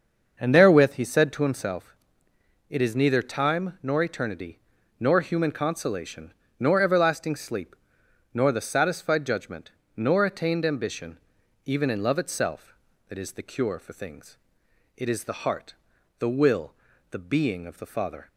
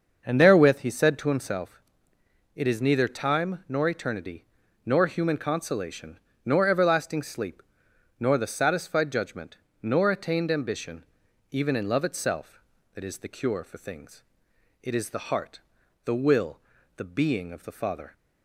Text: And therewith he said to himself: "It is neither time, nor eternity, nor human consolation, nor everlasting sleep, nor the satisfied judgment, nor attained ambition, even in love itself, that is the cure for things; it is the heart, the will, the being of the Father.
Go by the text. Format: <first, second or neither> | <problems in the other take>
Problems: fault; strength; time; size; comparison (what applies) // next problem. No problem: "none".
neither | starts louder than the rest; the same in both